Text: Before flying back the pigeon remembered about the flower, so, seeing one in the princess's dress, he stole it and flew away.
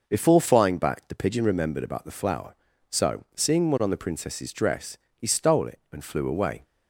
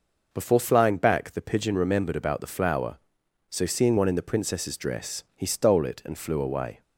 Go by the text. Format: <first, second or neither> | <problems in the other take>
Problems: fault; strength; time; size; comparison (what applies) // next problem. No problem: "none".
second | says "on" for "in"; at 3.8 s